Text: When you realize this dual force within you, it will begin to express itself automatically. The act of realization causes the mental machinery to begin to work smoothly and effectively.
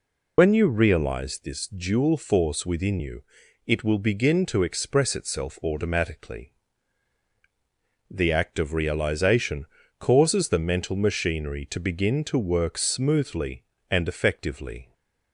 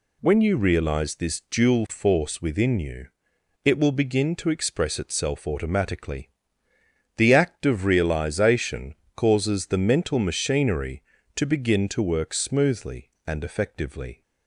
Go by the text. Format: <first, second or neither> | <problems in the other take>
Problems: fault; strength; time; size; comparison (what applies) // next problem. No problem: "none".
second | loses the start of "When"; at 0.3 s; 50 ms // pauses between "realization" and "causes"; slight; at 9.6 s; 0.32 s long; slight in the second